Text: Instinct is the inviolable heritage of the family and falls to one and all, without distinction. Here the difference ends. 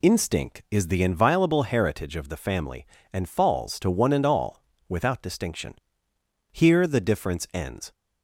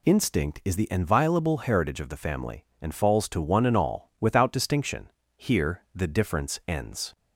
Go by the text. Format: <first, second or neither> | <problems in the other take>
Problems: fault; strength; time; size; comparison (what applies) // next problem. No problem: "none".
neither | none